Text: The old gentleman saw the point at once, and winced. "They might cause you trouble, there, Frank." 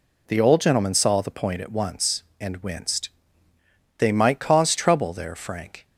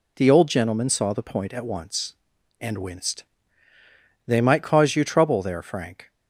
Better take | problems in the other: second | skips "you"; at 4.7 s

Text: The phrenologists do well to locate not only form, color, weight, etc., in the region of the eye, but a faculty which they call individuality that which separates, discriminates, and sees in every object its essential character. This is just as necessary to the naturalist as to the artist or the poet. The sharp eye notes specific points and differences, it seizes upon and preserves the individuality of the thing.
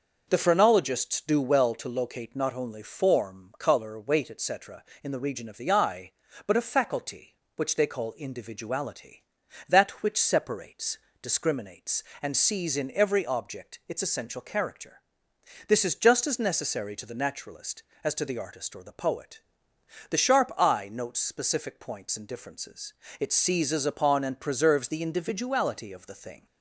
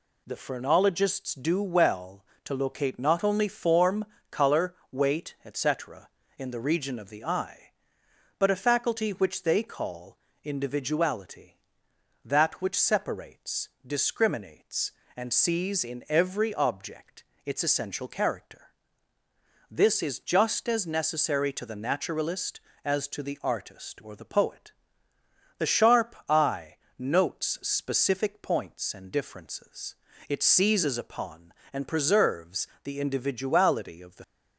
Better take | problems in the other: first | pauses between "call" and "individuality"; slight; at 10.1 s; 0.26 s long // pauses between "object" and "its"; slight; at 17.2 s; 0.22 s long // pauses between "eye" and "notes"; slight; at 26.7 s; 0.22 s long // pauses between "preserves" and "the"; slight; at 32.6 s; 0.18 s long // stops before "thing"; at 34.2 s

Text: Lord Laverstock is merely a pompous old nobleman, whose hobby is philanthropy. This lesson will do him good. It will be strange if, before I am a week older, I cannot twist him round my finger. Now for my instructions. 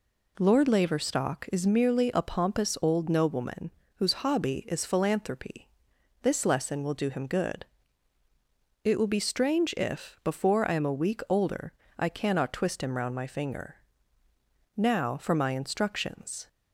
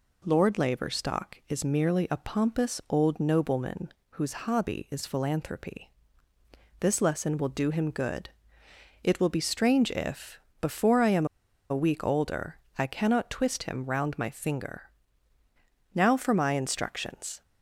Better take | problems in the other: first | pauses between "am" and "a"; at 11.2 s; 0.45 s long

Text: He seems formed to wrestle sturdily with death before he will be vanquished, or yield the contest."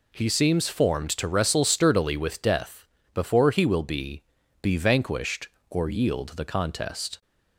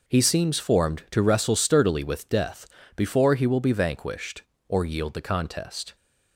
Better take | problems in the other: second | pauses between "death" and "before"; slight; at 2.8 s; 0.30 s long; slight in the second // says "be" twice; at 4.6 s

